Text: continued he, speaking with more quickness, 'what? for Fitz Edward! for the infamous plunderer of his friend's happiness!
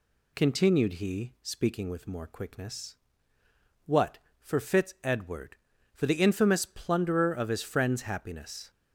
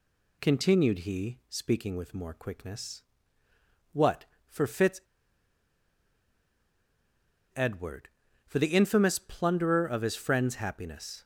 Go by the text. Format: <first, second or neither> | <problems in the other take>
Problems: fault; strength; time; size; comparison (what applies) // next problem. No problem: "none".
first | pauses between "Fitz" and "Edward"; strong; at 5.0 s; 2.5 s long